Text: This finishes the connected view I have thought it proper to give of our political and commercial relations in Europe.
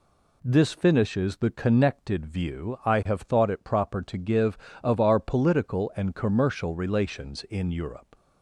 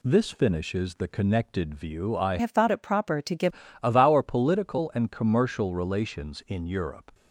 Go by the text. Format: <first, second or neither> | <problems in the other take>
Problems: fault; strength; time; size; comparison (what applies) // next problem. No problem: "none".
first | changes voice from "have" to "give"; from 2.3 to 3.5 s; 1.2 s long